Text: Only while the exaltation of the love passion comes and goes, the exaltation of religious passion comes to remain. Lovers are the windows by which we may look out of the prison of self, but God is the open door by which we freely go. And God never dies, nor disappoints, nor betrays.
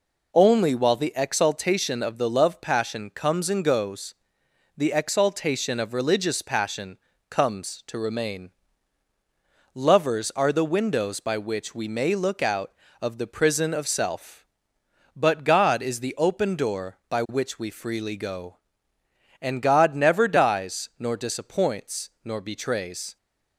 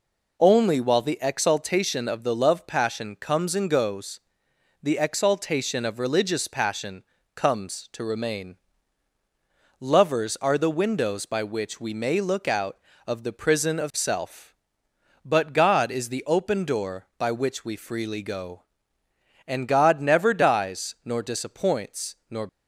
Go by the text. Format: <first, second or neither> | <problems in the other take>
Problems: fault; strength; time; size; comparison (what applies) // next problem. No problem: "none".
first | pauses between "passion" and "comes"; slight; at 7.0 s; 0.32 s long; slight in the first // stops before "betrays"; at 22.4 s